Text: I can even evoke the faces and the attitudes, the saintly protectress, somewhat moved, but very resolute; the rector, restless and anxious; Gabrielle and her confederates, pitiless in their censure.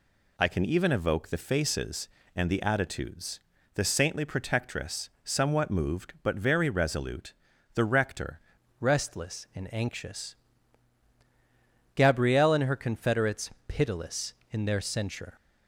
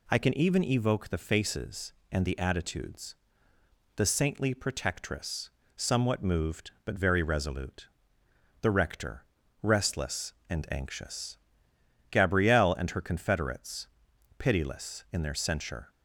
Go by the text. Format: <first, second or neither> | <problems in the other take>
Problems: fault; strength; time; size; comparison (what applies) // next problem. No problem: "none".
second | changes voice at "restless"; from 8.8 s on; 6.5 s long